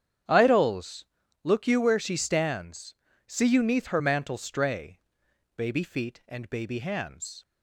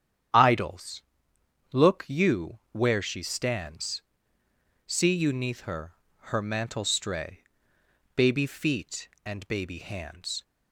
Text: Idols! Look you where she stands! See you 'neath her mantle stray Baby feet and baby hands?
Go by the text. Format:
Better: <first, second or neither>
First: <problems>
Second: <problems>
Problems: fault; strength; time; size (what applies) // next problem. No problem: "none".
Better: first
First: starts louder than the rest; strong; until 1.6 s; 9 dB // pauses between "stray" and "Baby"; noticeable; at 4.9 s; 0.56 s long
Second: starts louder than the rest; strong; until 2.0 s; 9.5 dB // says "her" twice; at 6.3 s // pauses between "stray" and "Baby"; noticeable; at 7.4 s; 0.72 s long